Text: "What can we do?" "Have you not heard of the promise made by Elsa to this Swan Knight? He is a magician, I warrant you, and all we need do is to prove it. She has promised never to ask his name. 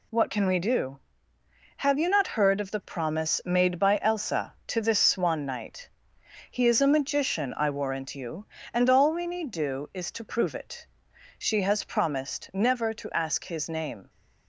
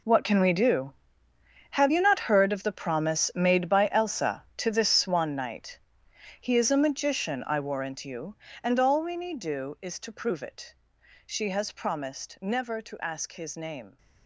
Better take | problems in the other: first | gets quieter; strong; throughout; 15 dB

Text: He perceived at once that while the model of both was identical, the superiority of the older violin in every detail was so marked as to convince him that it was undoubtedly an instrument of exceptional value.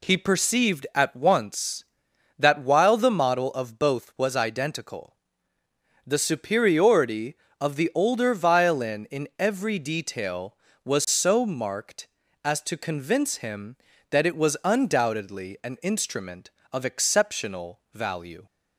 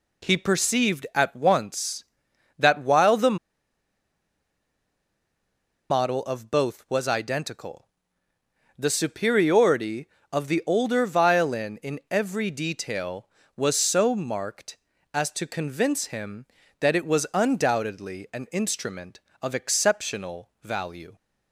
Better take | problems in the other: first | pauses between "the" and "model"; strong; at 3.3 s; 2.5 s long

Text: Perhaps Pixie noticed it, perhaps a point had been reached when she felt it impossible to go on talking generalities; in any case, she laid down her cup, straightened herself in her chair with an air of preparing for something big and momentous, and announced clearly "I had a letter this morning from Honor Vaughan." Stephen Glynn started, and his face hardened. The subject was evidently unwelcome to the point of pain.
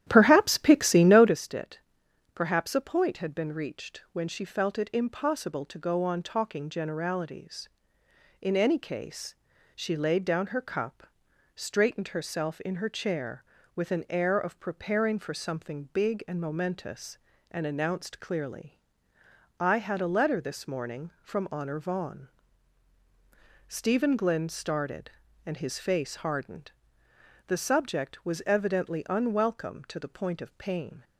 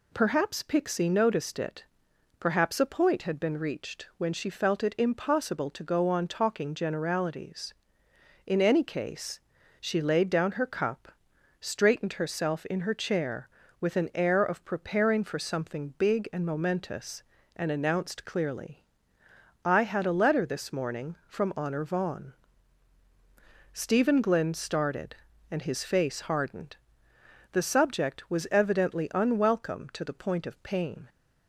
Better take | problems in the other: second | starts louder than the rest; strong; until 1.4 s; 11.5 dB // pauses between "clearly" and "I"; noticeable; at 18.7 s; 0.80 s long; noticeable in the second

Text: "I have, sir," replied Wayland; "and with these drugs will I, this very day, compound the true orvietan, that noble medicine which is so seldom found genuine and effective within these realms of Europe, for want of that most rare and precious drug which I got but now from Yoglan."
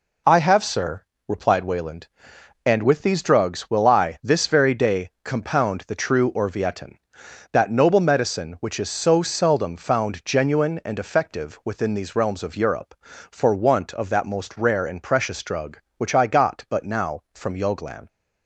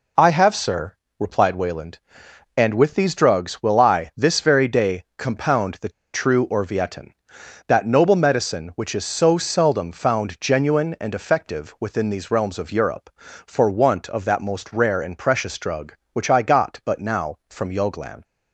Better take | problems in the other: first | pauses between "the" and "true"; slight; at 5.8 s; 0.24 s long

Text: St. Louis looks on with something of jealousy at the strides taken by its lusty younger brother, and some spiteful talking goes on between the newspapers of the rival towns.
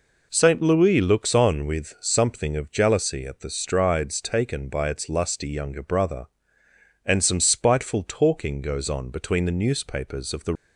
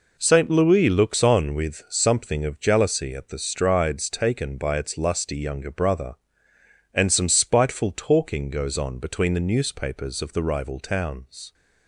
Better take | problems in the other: second | stops before "rival towns"; at 10.5 s

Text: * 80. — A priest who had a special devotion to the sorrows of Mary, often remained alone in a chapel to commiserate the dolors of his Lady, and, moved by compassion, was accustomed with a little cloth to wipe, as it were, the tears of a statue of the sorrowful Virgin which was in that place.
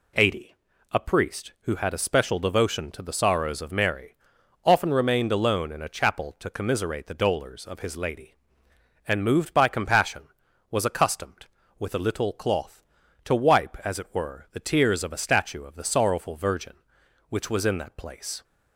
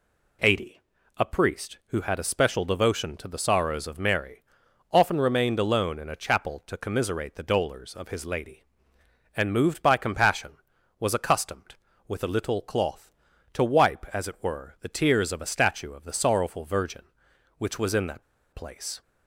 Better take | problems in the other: first | pauses between "that" and "place"; slight; at 18.2 s; 0.30 s long

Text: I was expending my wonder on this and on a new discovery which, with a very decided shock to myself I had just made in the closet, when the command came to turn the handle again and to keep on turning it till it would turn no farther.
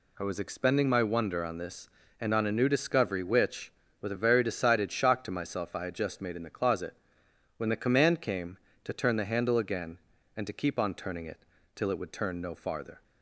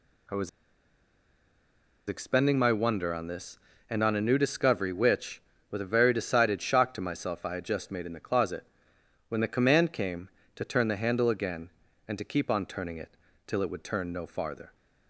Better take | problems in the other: first | pauses between "was" and "expending"; strong; at 0.4 s; 1.5 s long // pauses between "it" and "till"; slight; at 13.1 s; 0.28 s long; slight in the first

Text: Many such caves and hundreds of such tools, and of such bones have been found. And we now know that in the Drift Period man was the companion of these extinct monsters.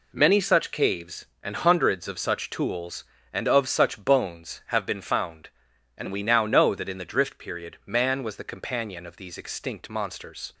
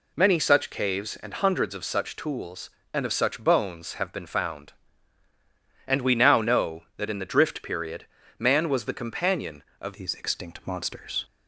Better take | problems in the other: first | pauses between "Period" and "man"; slight; at 8.0 s; 0.32 s long // changes voice at "these"; from 9.9 s on; 1.3 s long

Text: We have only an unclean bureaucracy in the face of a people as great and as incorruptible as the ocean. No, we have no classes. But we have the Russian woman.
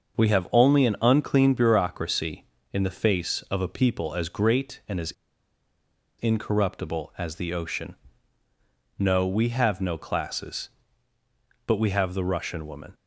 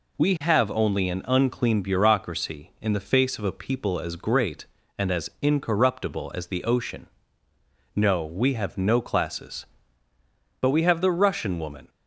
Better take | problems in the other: second | starts louder than the rest; until 1.2 s; 6.5 dB // pauses between "as" and "incorruptible"; at 5.1 s; 1.0 s long

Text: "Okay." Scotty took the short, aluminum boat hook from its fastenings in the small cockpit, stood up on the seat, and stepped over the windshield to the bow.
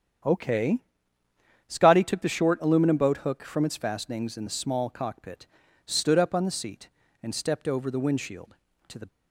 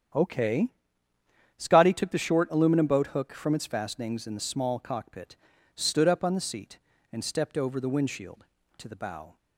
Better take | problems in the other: second | starts louder than the rest; strong; until 2.1 s; 8.5 dB; strong in the second // stops before "bow"; at 9.0 s

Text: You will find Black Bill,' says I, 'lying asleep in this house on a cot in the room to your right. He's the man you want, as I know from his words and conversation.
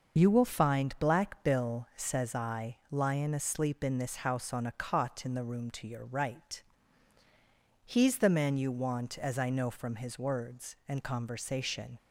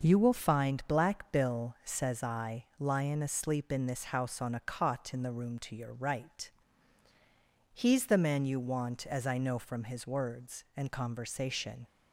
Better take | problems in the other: second | loses the start of "You"; at 0.1 s; 35 ms // starts louder than the rest; noticeable; until 1.2 s; 6 dB; noticeable in the second

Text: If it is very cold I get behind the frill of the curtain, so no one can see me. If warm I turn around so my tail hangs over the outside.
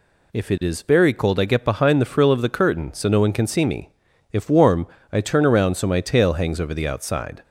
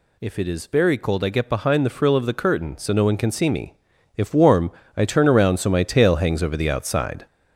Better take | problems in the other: first | gets louder; noticeable; throughout; 5.5 dB // pauses between "warm" and "I"; slight; at 4.7 s; 0.24 s long; slight in the first

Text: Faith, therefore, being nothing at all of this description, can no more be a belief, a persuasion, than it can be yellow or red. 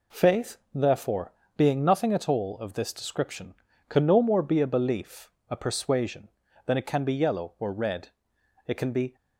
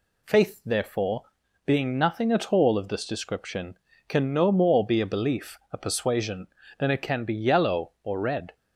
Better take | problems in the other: second | goes on to say "It can be"; slight; from 8.6 s on; 0.48 s long

